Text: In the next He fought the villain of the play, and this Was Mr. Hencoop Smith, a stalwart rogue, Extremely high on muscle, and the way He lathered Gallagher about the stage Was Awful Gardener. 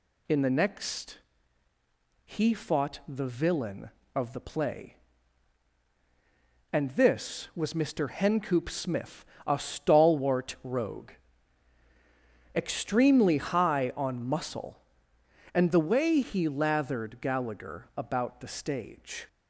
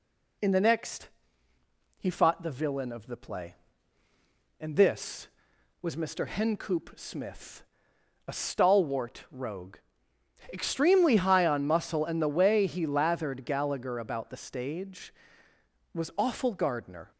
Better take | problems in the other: second | pauses between "next" and "He"; at 1.1 s; 1.0 s long; noticeable in the second // stops before "Was Awful Gardener"; at 19.2 s

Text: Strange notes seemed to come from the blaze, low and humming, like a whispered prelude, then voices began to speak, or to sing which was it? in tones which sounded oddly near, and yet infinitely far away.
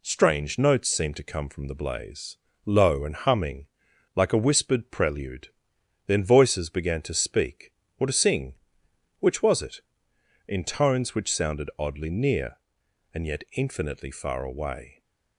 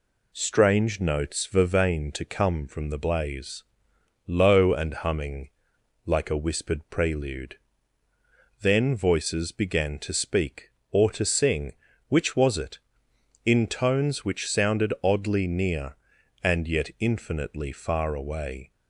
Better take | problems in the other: first | says "vervain" for "seemed"; at 1.4 s

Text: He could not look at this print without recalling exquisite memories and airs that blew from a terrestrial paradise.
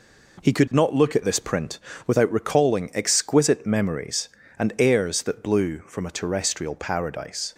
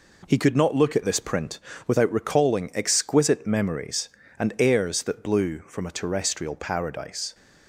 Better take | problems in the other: neither | pauses between "print" and "without"; slight; the same in both

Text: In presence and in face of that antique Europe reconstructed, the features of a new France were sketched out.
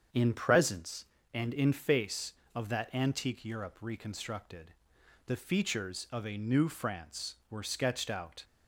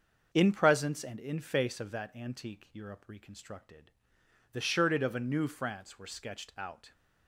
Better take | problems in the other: first | starts louder than the rest; until 1.3 s; 6.5 dB; strong in the first // says "shirted" for "features"; at 4.6 s

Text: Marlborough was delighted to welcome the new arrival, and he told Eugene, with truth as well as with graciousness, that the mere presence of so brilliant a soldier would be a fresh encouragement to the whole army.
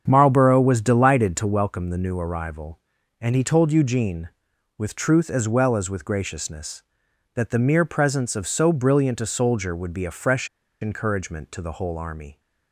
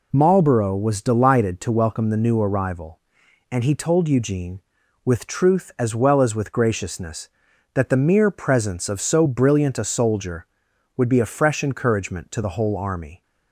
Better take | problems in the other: second | starts louder than the rest; strong; until 1.0 s; 7.5 dB // pauses between "fresh" and "encouragement"; slight; at 10.4 s; 0.33 s long

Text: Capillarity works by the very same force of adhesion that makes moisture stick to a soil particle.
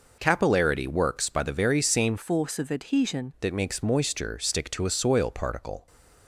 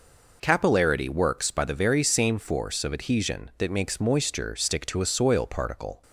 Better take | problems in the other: second | changes voice from "force" to "adhesion"; from 2.1 to 3.3 s; 1.2 s long

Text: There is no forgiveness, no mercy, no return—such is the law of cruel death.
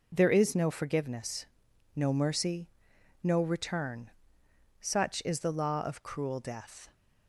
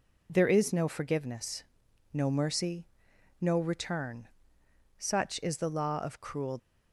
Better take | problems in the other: first | stops before "death"; at 6.5 s

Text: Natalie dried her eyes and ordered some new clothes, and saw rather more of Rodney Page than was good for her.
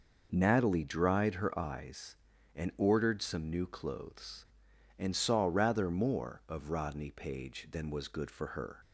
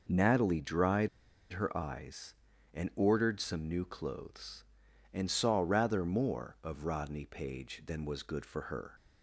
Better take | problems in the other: first | pauses between "dried" and "her"; at 1.0 s; 0.44 s long

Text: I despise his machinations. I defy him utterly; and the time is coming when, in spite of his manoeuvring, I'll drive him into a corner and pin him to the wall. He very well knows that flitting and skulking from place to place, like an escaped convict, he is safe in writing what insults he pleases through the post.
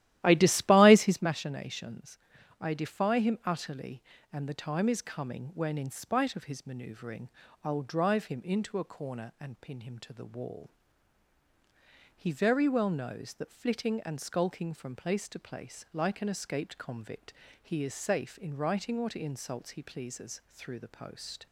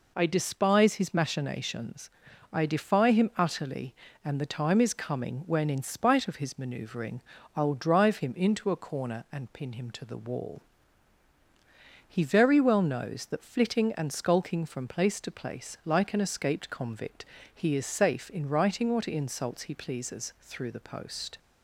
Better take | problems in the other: second | starts louder than the rest; strong; until 1.3 s; 14 dB

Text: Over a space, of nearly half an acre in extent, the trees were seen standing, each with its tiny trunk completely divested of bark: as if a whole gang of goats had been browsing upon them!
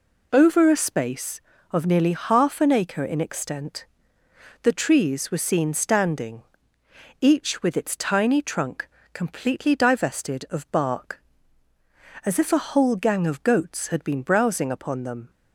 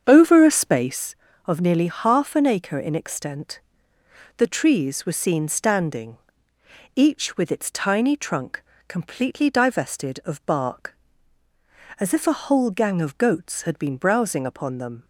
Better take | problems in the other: first | starts louder than the rest; strong; until 1.2 s; 7.5 dB // pauses between "trunk" and "completely"; slight; at 8.6 s; 0.26 s long; slight in the first

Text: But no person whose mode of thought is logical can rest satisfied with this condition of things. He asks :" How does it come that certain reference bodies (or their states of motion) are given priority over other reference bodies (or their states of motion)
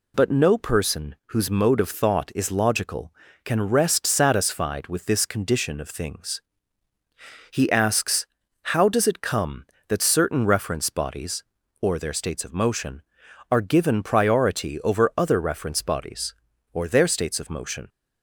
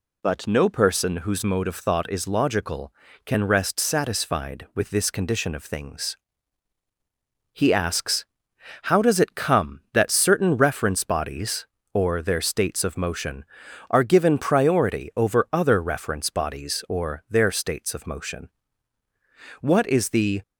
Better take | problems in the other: first | goes on to say "What is the"; noticeable; from 19.6 s on; 0.80 s long

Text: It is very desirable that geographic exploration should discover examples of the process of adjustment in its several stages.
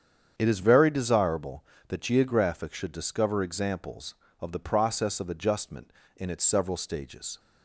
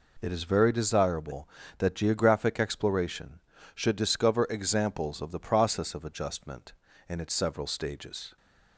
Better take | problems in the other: second | starts louder than the rest; strong; until 1.3 s; 8 dB // skips "exploration"; at 2.7 s

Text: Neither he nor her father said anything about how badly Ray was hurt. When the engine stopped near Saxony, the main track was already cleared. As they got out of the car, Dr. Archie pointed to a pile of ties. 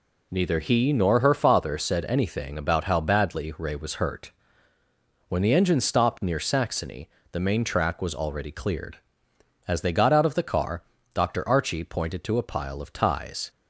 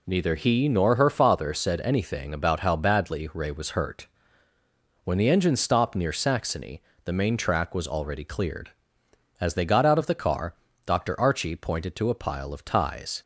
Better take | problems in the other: neither | none

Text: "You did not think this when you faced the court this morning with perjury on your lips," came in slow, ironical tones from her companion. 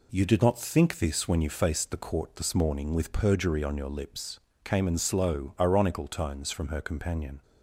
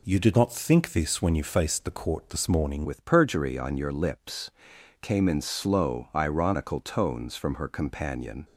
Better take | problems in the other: first | changes voice at "with"; from 2.8 s on; 5.6 s long

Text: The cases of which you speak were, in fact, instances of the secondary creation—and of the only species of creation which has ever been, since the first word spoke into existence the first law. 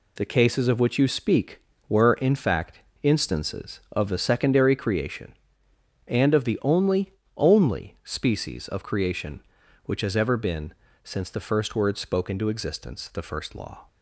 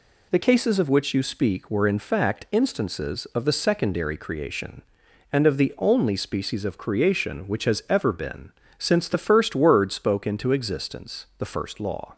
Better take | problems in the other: second | says "only" twice; at 7.3 s

